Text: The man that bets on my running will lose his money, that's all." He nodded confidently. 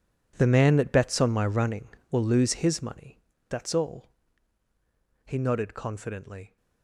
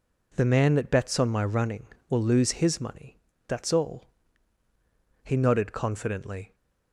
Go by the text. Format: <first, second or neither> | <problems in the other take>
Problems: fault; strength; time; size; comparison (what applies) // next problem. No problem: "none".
second | gets quieter; strong; throughout; 16.5 dB